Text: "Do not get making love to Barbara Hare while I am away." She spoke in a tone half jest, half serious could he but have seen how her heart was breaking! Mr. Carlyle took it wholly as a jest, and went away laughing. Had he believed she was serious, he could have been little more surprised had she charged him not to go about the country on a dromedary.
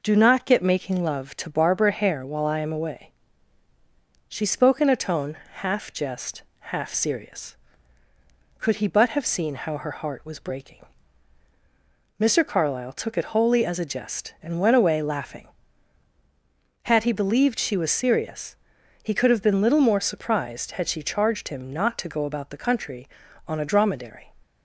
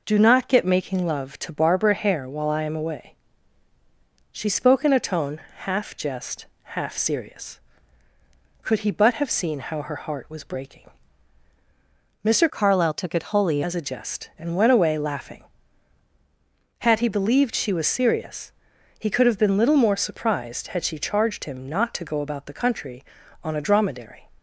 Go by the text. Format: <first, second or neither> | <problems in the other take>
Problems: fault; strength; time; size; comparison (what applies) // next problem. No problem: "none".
first | pauses between "tone" and "half"; slight; at 5.3 s; 0.20 s long; slight in the first // changes voice from "Carlyle" to "wholly"; from 12.4 to 13.6 s; 1.2 s long